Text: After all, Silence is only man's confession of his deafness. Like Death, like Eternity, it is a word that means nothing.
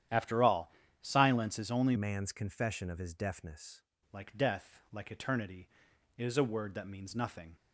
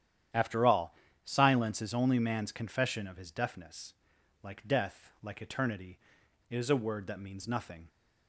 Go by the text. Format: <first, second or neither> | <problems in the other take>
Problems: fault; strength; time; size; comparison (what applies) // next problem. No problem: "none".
second | starts louder than the rest; strong; until 1.4 s; 10.5 dB; strong in the second // changes voice from "man's" to "deafness"; from 1.9 to 3.8 s; 1.9 s long